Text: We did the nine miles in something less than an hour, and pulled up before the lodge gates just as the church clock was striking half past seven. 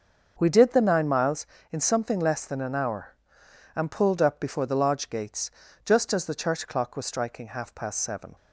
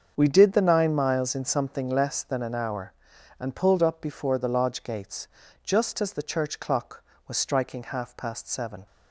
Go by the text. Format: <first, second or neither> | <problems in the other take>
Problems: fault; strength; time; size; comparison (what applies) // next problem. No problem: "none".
neither | starts louder than the rest; the same in both // pauses between "gates" and "just"; the same in both